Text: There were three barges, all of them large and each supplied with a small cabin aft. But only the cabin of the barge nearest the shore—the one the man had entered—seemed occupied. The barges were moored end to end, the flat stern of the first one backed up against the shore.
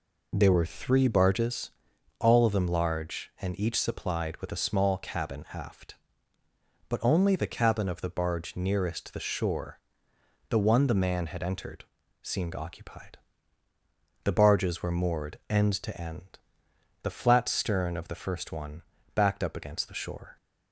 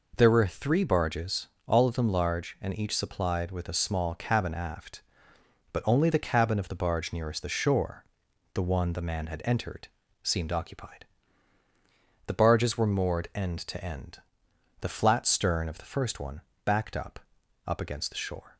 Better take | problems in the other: first | pauses between "one" and "backed"; slight; at 16.4 s; 0.24 s long; slight in the first // says "up" twice; at 17.6 s

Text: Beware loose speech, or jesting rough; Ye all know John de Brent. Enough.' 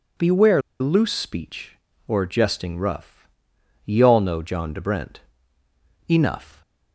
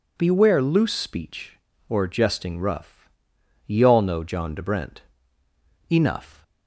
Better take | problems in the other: second | pauses between "Beware" and "loose"; slight; at 0.6 s; 0.20 s long

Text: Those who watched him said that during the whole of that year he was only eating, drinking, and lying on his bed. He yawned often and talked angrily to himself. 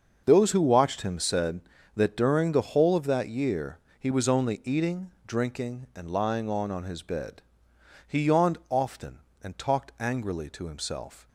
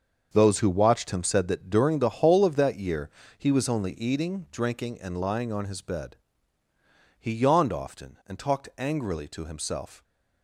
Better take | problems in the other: second | starts louder than the rest; until 1.2 s; 6.5 dB; also in the second // pauses between "year" and "he"; slight; at 3.7 s; 0.20 s long; slight in the second // says "on" twice; at 6.7 s

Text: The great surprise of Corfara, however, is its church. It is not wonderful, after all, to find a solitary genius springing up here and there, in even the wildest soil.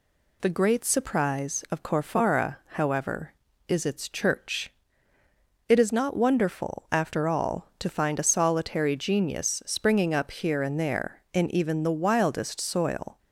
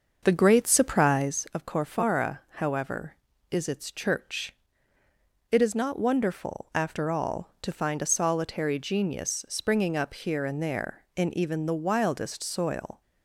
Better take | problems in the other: first | starts louder than the rest; until 1.5 s; 6.5 dB

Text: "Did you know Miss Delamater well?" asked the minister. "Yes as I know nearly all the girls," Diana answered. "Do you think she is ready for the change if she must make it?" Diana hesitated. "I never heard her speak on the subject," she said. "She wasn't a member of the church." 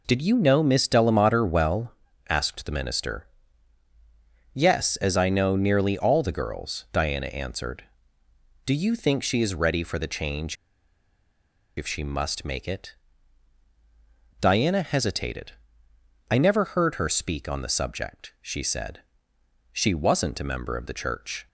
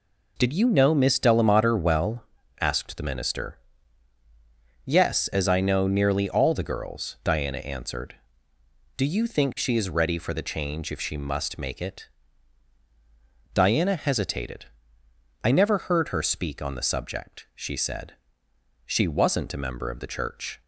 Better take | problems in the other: second | pauses between "change" and "if"; at 10.5 s; 1.2 s long

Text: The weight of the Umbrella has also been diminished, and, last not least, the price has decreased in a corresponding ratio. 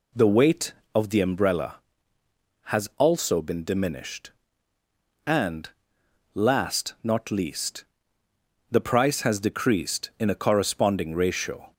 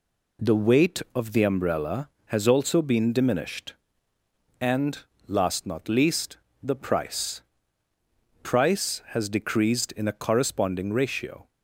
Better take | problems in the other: first | says "price" twice; at 8.4 s

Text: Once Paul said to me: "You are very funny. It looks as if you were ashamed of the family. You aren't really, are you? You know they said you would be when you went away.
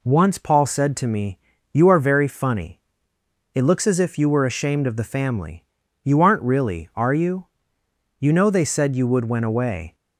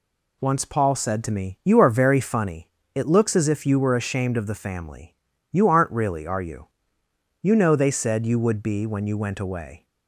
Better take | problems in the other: second | skips "be when you"; at 9.2 s

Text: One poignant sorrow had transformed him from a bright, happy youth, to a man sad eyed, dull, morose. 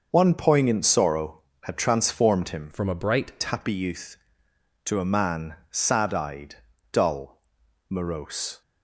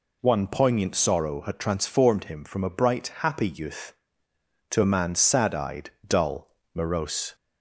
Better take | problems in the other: second | starts louder than the rest; noticeable; until 1.1 s; 6 dB // changes voice from "from" to "bright"; from 2.7 to 3.3 s; 0.6 s long // pauses between "man" and "sad"; slight; at 5.5 s; 0.16 s long

